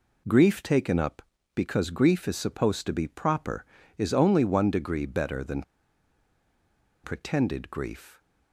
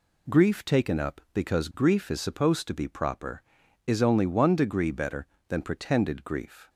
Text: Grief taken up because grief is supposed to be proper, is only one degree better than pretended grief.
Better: second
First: pauses between "than" and "pretended"; strong; at 5.6 s; 1.4 s long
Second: none

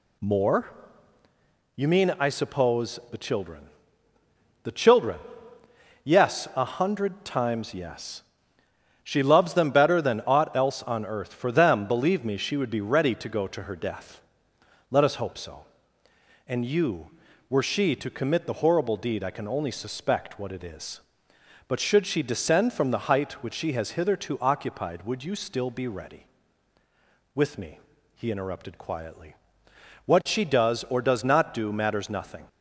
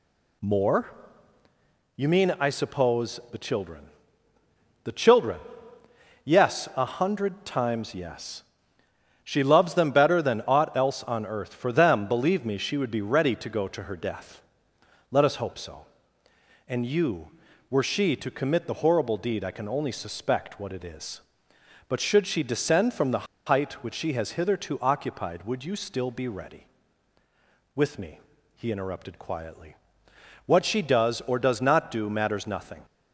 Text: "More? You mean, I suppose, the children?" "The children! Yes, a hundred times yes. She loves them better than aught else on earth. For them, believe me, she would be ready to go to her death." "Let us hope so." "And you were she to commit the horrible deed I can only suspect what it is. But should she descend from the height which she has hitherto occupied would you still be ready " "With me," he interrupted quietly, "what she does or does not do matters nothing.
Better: first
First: none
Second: pauses between "the" and "height"; slight; at 23.2 s; 0.20 s long

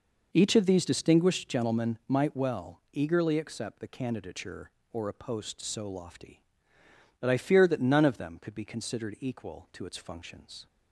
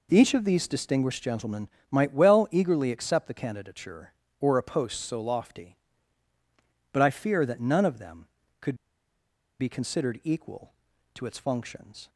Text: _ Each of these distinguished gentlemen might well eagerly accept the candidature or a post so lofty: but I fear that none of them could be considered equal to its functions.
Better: first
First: none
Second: pauses between "gentlemen" and "might"; slight; at 1.6 s; 0.24 s long // pauses between "could" and "be"; noticeable; at 8.7 s; 0.85 s long

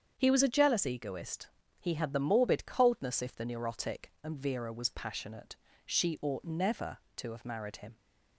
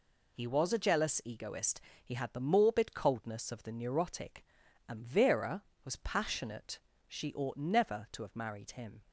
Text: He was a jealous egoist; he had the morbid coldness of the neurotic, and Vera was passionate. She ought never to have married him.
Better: second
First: starts louder than the rest; strong; until 1.1 s; 7.5 dB // says "if" for "of"; at 3.2 s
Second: none

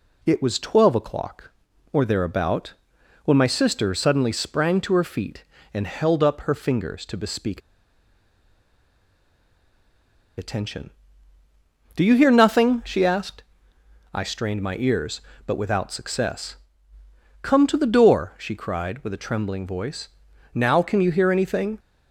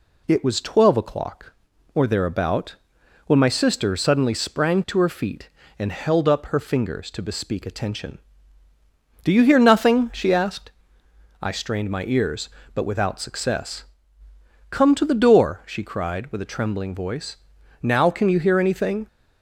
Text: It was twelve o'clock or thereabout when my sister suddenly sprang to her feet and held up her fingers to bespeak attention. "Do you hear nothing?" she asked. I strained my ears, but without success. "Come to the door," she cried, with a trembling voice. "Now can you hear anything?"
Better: second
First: pauses between "thereabout" and "when"; noticeable; at 2.7 s; 0.50 s long // pauses between "bespeak" and "attention"; strong; at 7.5 s; 2.7 s long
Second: pauses between "thereabout" and "when"; noticeable; at 2.7 s; 0.50 s long

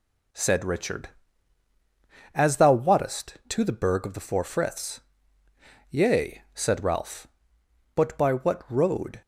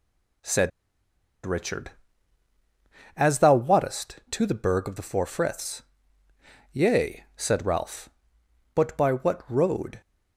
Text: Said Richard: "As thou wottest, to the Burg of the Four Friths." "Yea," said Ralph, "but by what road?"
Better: first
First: none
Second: pauses between "Said" and "Richard"; noticeable; at 0.7 s; 0.74 s long

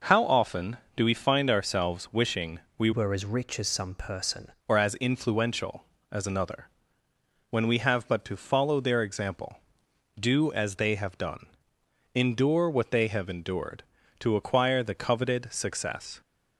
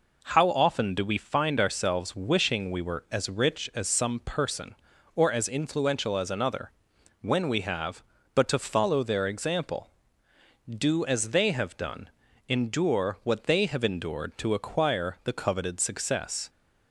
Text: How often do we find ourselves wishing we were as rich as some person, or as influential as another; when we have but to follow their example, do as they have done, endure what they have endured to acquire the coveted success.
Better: second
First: pauses between "wishing" and "we"; slight; at 2.5 s; 0.18 s long // changes voice from "were" to "person"; from 2.9 to 4.5 s; 1.6 s long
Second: none

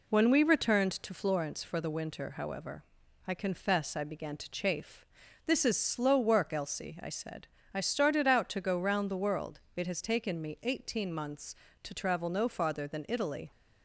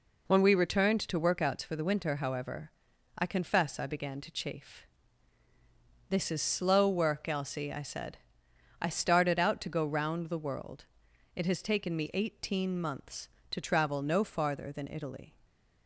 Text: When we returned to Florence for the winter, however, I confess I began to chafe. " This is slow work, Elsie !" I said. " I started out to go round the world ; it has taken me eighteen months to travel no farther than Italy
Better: first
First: none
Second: says "Workouts" for "Florence"; at 1.2 s // stays silent after the last word; slight; from 15.2 s on; 0.6 s long

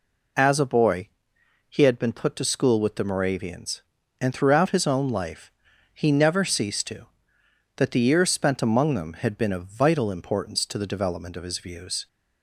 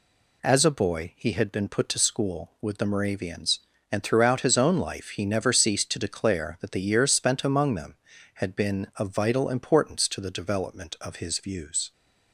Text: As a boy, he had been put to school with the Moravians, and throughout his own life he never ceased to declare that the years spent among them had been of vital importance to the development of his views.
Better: second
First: pauses between "life" and "he"; at 5.5 s; 0.42 s long // skips "declare"; at 7.4 s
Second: none

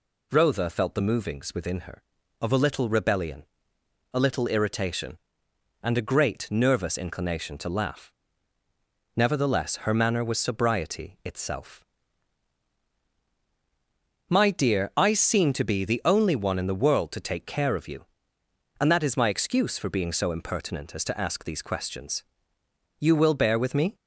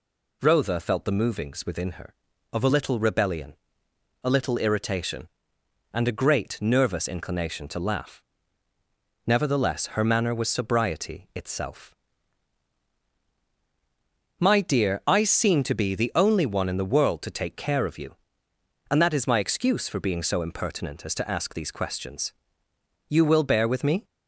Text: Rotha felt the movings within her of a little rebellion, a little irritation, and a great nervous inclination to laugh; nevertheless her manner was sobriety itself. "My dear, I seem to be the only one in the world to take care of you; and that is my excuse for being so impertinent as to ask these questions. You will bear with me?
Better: neither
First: none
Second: none

